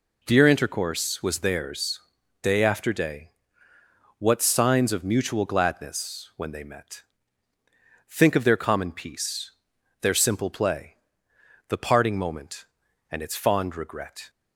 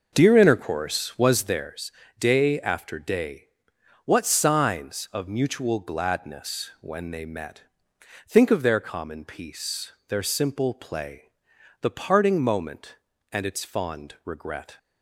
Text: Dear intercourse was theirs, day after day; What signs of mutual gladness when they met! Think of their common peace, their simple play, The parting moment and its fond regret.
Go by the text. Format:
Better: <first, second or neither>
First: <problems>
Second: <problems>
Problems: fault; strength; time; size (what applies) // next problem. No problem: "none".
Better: first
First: none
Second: starts louder than the rest; noticeable; until 1.8 s; 5.5 dB